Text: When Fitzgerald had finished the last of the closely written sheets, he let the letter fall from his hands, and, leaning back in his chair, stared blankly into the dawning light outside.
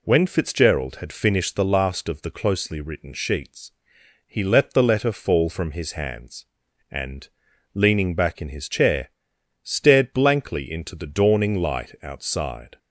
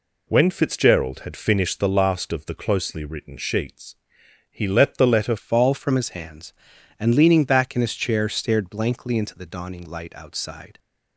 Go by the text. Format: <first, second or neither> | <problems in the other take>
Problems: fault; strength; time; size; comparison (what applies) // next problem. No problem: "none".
first | changes voice at "fall"; from 5.3 s on; 5.4 s long